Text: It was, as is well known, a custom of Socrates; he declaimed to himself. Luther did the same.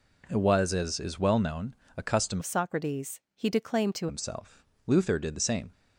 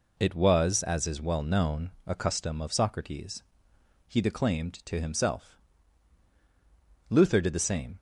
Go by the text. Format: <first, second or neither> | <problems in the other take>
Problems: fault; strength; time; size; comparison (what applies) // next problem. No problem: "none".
second | changes voice from "of" to "to"; from 2.3 to 4.0 s; 1.7 s long